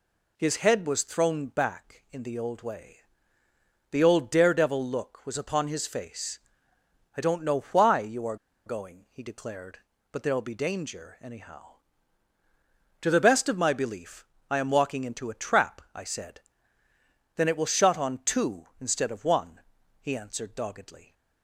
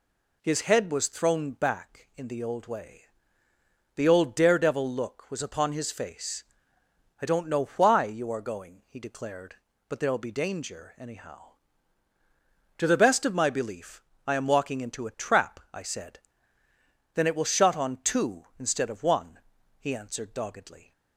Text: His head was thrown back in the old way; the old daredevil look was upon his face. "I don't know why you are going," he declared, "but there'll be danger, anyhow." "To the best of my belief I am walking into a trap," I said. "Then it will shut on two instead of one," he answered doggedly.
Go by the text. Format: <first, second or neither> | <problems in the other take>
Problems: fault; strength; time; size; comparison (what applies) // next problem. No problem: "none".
second | pauses between "are" and "going"; slight; at 8.3 s; 0.30 s long // pauses between "belief" and "I"; slight; at 14.2 s; 0.24 s long; slight in the second